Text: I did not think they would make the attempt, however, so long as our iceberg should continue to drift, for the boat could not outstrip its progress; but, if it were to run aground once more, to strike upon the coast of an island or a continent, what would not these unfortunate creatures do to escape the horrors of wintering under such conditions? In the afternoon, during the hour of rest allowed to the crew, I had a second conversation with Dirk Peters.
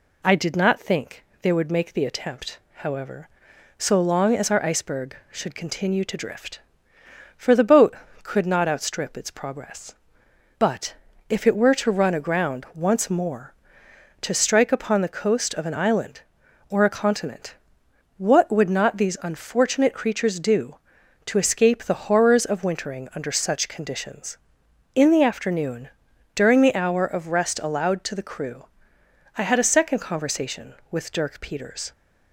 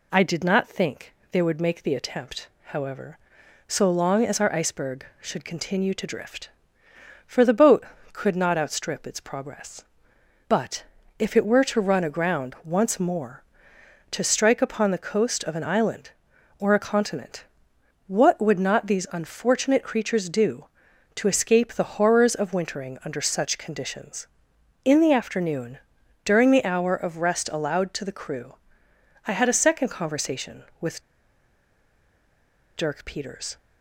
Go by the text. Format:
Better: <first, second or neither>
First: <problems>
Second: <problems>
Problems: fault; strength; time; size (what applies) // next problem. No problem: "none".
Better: first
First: pauses between "think" and "they"; slight; at 1.2 s; 0.18 s long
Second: pauses between "think" and "they"; slight; at 1.1 s; 0.18 s long // pauses between "with" and "Dirk"; strong; at 31.0 s; 1.7 s long